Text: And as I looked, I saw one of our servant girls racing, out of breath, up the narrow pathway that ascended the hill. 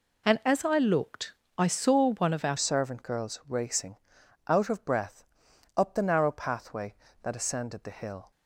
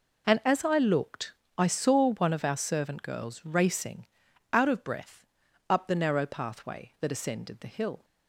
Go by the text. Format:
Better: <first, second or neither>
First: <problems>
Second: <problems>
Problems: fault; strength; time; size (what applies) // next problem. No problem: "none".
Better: second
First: changes voice at "servant"; from 2.5 s on; 5.8 s long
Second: none